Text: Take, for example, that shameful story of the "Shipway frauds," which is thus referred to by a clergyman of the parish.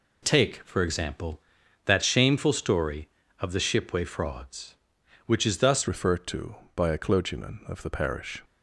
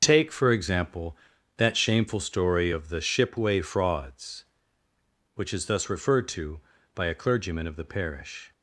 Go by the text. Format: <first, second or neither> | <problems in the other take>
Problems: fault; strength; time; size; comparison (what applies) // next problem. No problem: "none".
second | changes voice at "referred"; from 5.8 s on; 2.6 s long